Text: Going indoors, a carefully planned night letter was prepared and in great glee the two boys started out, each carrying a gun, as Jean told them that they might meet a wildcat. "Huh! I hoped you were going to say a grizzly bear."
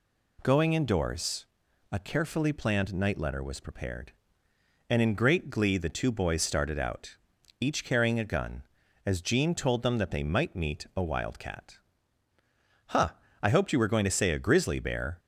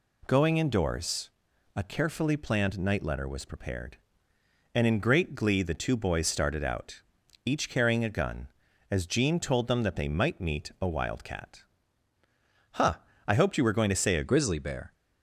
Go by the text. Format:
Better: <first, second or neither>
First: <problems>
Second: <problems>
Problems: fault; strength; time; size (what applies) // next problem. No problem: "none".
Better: first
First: none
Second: changes voice at "grizzly"; from 14.2 s on; 0.7 s long